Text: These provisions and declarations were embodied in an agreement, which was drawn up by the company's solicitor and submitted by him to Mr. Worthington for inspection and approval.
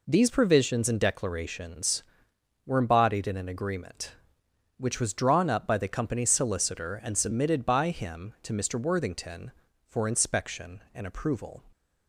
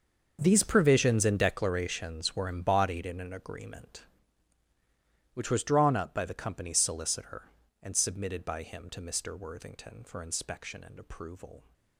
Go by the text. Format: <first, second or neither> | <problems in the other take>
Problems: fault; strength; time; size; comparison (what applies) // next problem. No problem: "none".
first | gets quieter; strong; throughout; 15.5 dB